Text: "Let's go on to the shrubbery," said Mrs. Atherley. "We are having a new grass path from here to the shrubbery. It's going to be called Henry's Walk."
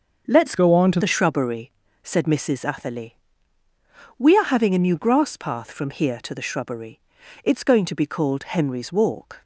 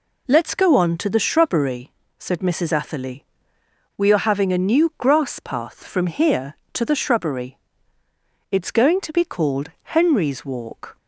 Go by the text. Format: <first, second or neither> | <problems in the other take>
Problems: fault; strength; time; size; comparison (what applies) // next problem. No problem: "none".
second | starts louder than the rest; until 1.3 s; 6.5 dB // changes voice from "go" to "to"; from 0.5 to 0.9 s; 0.4 s long